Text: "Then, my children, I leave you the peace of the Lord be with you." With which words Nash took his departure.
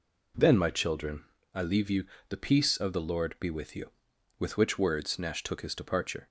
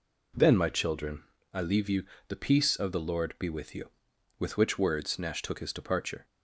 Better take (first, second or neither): neither